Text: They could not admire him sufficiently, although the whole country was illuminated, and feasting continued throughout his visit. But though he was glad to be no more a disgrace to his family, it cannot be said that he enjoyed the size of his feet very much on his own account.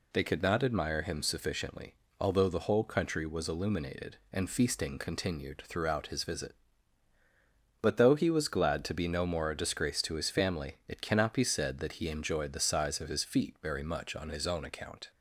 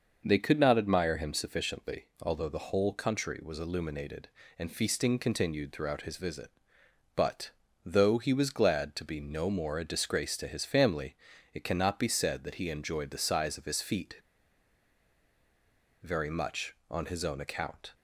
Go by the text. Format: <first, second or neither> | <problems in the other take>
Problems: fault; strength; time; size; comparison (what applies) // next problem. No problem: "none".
first | starts louder than the rest; noticeable; until 1.2 s; 6 dB // pauses between "But" and "though"; slight; at 7.4 s; 0.34 s long // pauses between "feet" and "very"; strong; at 14.1 s; 1.8 s long